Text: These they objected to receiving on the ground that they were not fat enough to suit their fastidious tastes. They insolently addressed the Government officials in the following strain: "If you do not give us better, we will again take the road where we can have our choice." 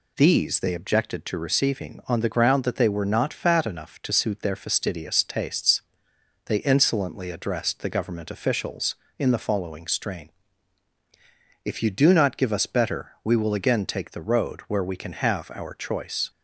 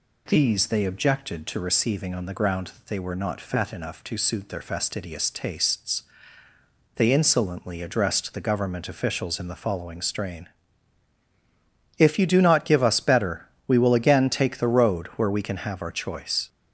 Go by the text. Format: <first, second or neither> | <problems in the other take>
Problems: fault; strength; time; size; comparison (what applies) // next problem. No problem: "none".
neither | none